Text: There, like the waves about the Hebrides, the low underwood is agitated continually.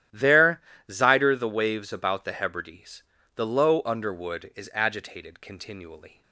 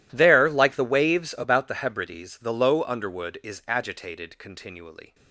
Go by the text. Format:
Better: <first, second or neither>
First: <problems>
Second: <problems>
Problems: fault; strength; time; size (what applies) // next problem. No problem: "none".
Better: second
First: starts louder than the rest; strong; until 1.3 s; 12 dB // says "zider" for "like"; at 0.9 s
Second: none